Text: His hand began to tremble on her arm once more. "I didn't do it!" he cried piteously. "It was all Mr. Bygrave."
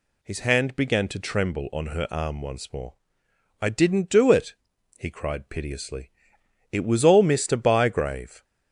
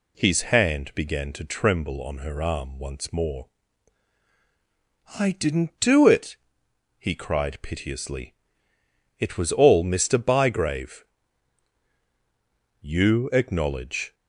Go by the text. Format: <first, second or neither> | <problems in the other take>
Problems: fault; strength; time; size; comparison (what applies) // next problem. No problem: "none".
first | goes on to say "You acknowledge"; from 12.7 s on; 1.3 s long